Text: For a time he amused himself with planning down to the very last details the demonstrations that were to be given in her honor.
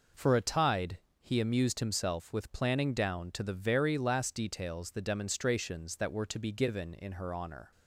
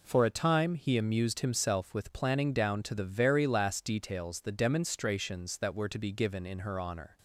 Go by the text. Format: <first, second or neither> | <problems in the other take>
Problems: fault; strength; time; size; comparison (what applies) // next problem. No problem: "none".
second | says "tide" for "time"; at 0.4 s